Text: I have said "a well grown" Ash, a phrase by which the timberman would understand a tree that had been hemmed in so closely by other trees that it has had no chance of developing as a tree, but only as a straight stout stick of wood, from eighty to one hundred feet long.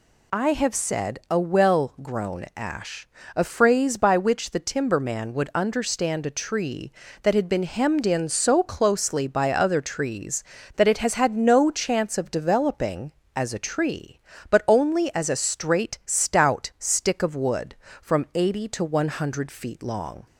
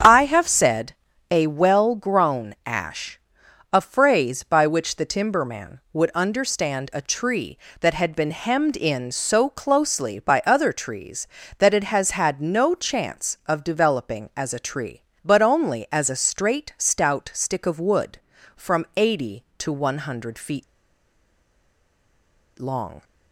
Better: first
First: none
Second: starts louder than the rest; strong; until 1.3 s; 7.5 dB // pauses between "said" and "a"; slight; at 0.9 s; 0.34 s long // pauses between "feet" and "long"; strong; at 20.6 s; 1.9 s long

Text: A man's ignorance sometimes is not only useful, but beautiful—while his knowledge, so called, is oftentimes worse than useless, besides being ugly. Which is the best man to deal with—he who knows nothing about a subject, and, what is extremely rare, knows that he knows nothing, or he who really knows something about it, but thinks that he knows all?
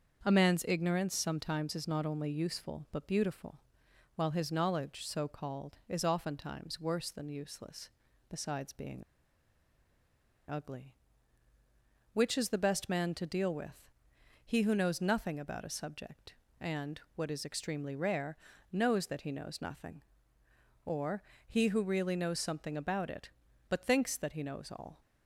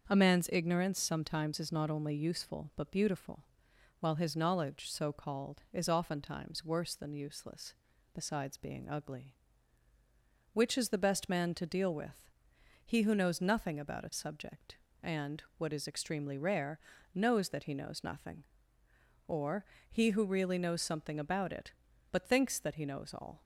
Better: second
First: starts louder than the rest; until 1.2 s; 6.5 dB // pauses between "being" and "ugly"; strong; at 9.0 s; 1.4 s long // pauses between "or" and "he"; slight; at 21.2 s; 0.28 s long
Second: starts louder than the rest; until 1.1 s; 6.5 dB // pauses between "or" and "he"; slight; at 19.6 s; 0.28 s long

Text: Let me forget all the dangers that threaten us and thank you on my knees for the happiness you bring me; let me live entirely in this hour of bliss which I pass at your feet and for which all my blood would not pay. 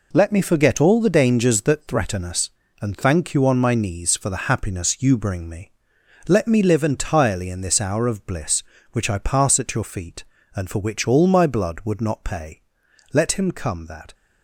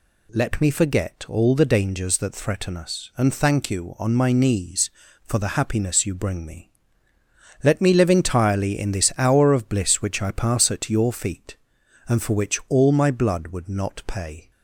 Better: second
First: goes on to say "Let him come that"; noticeable; from 13.1 s on; 1.0 s long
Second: none

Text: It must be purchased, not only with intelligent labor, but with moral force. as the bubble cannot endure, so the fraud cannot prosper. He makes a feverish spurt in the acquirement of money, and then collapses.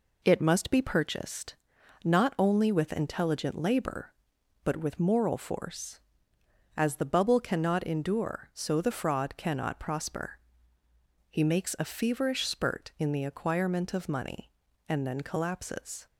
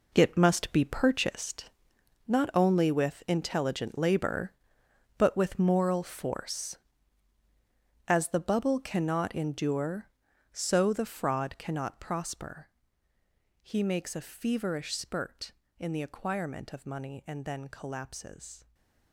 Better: first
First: none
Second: gets quieter; strong; throughout; 11 dB // stays silent after the last word; slight; from 18.5 s on; 0.6 s long

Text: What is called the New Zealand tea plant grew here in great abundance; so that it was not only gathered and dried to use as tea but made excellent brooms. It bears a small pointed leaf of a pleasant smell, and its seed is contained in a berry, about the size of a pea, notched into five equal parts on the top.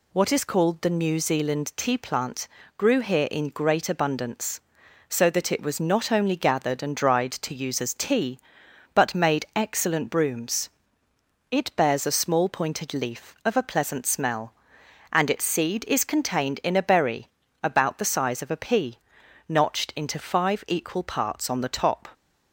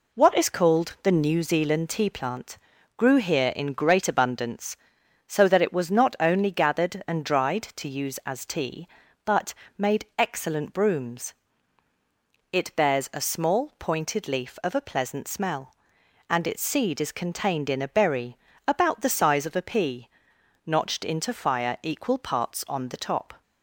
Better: first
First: pauses between "plant" and "grew"; slight; at 2.4 s; 0.30 s long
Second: pauses between "plant" and "grew"; at 2.5 s; 0.40 s long // pauses between "but" and "made"; slight; at 9.5 s; 0.24 s long // says "fire" for "five"; at 21.3 s

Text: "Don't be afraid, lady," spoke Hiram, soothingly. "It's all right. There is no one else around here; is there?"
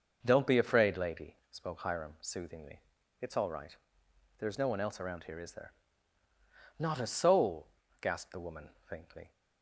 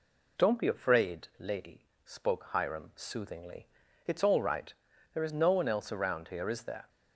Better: second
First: goes on to say "Not a soul gasped the woman faintly"; strong; from 6.7 s on; 2.5 s long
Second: none

